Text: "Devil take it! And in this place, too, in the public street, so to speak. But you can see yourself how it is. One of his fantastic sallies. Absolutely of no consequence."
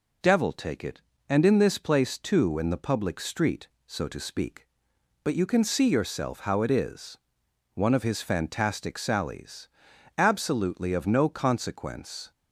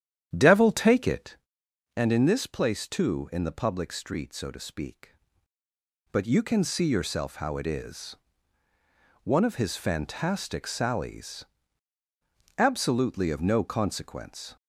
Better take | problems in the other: first | starts louder than the rest; strong; until 1.5 s; 9.5 dB

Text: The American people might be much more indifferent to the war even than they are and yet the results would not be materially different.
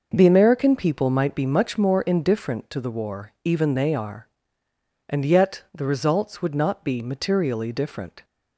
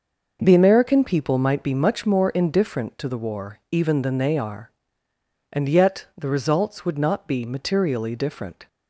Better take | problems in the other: second | skips "than"; at 3.7 s

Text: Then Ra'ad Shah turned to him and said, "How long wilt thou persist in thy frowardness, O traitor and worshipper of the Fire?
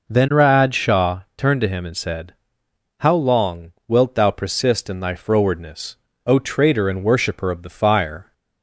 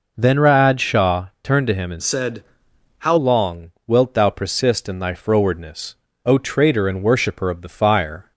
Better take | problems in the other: first | pauses between "Shah" and "turned"; slight; at 1.2 s; 0.16 s long; slight in the first // changes voice from "said" to "How"; from 2.0 to 3.1 s; 1.1 s long

